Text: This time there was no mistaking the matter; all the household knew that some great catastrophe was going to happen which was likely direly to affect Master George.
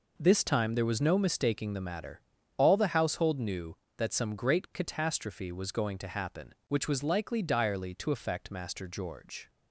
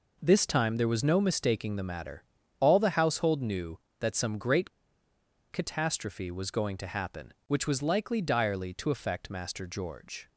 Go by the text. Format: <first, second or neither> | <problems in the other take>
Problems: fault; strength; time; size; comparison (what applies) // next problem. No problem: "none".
first | pauses between "great" and "catastrophe"; noticeable; at 4.6 s; 0.82 s long